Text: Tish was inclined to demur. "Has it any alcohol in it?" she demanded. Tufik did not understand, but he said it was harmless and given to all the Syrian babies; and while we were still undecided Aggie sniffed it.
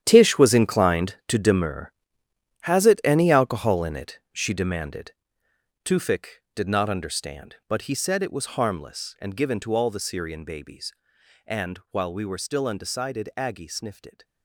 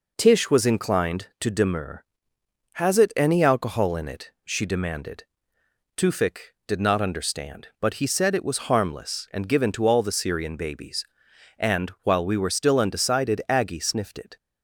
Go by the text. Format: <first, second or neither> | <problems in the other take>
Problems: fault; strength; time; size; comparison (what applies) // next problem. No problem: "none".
second | gets quieter; strong; throughout; 13 dB